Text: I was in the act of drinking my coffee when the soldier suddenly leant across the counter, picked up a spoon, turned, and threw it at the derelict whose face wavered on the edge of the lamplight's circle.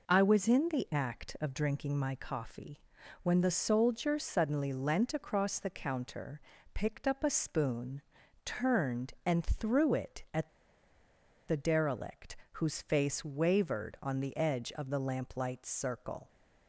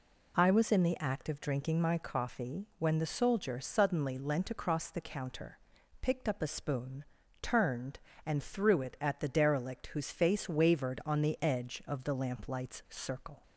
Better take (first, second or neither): second